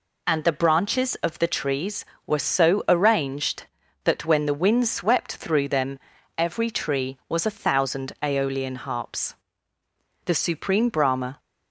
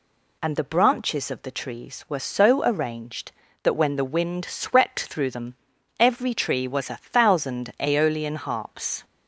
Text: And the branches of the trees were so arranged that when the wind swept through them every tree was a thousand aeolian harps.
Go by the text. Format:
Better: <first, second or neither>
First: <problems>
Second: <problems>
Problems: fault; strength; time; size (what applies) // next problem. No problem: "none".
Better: second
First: pauses between "them" and "every"; at 5.9 s; 0.38 s long // goes on to say "The Supreme Brahma"; noticeable; from 10.2 s on; 1.1 s long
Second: pauses between "them" and "every"; at 5.5 s; 0.44 s long